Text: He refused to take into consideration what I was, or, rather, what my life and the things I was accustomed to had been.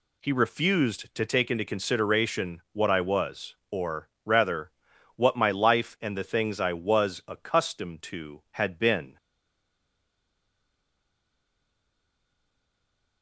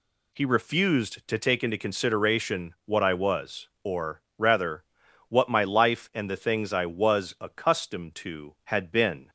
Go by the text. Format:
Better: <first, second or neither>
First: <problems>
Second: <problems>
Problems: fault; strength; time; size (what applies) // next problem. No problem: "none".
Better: second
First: stays silent after the last word; strong; from 9.1 s on; 4.1 s long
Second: none